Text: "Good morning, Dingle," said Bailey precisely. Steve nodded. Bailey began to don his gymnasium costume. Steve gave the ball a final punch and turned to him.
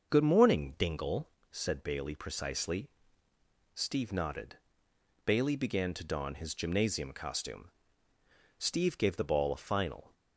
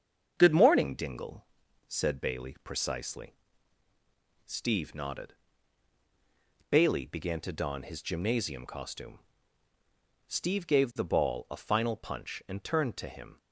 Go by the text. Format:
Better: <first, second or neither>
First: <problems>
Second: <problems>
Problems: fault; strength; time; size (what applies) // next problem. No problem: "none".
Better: second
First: starts louder than the rest; until 1.1 s; 6.5 dB // stops before "punch and turned to him"; at 10.1 s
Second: starts louder than the rest; until 1.3 s; 7 dB